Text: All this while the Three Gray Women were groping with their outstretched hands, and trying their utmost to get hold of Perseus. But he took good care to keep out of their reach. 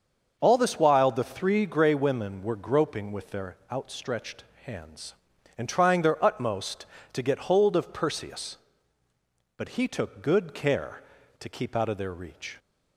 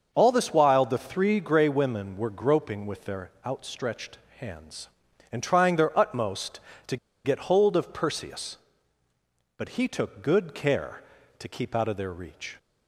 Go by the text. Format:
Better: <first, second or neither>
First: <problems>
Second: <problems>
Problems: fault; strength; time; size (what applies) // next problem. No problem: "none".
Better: first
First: starts louder than the rest; until 1.4 s; 6.5 dB // pauses between "their" and "outstretched"; slight; at 3.5 s; 0.16 s long // pauses between "outstretched" and "hands"; slight; at 4.4 s; 0.20 s long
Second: starts louder than the rest; until 1.1 s; 6.5 dB // pauses between "their" and "outstretched"; slight; at 3.2 s; 0.16 s long // pauses between "outstretched" and "hands"; slight; at 4.1 s; 0.20 s long // pauses between "to" and "get"; slight; at 6.9 s; 0.29 s long